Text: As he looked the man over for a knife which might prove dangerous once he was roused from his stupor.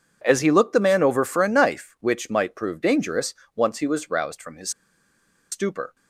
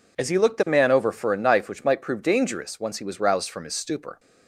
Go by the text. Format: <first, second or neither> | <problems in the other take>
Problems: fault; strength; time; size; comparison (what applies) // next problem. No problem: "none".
second | pauses between "dangerous" and "once"; slight; at 3.3 s; 0.22 s long // pauses between "his" and "stupor"; noticeable; at 4.7 s; 0.81 s long